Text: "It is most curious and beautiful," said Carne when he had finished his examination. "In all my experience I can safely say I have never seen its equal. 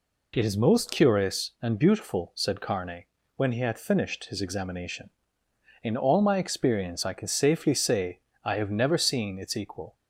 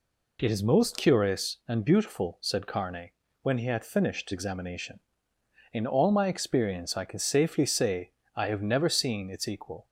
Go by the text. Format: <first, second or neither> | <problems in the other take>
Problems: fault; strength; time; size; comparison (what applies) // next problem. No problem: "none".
first | pauses between "Carne" and "when"; slight; at 3.1 s; 0.32 s long; slight in the first // skips "his"; at 4.3 s // pauses between "say" and "I"; slight; at 8.1 s; 0.22 s long; slight in the first